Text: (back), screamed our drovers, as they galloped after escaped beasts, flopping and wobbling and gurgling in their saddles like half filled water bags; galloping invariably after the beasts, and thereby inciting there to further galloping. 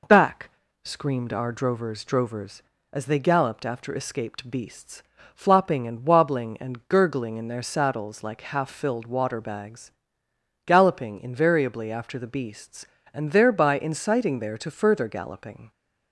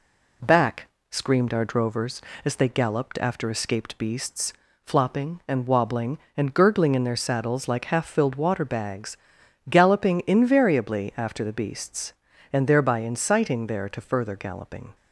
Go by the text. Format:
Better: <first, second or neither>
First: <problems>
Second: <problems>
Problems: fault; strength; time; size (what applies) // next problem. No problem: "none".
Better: second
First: says "drovers" twice; at 2.0 s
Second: none